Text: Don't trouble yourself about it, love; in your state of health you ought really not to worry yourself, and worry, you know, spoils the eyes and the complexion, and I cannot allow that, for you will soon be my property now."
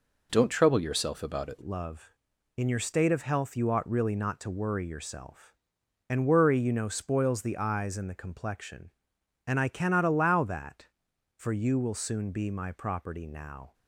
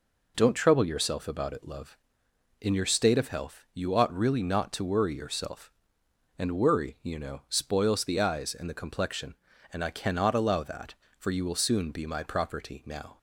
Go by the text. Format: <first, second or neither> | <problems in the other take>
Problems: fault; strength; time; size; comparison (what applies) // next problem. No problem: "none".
second | changes voice at "love"; from 1.6 s on; 12.1 s long